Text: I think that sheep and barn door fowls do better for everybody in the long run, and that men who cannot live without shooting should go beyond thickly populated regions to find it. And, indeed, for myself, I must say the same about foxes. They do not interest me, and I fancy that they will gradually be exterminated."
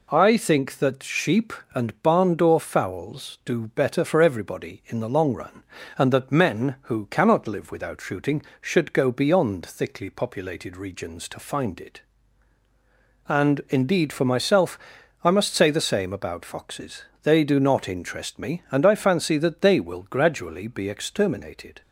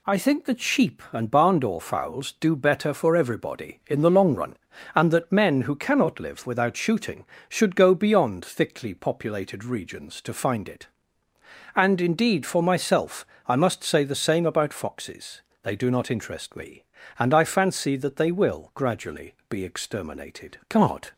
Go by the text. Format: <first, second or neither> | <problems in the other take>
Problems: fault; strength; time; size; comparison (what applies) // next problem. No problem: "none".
first | goes on to say "God"; slight; from 20.6 s on; 0.46 s long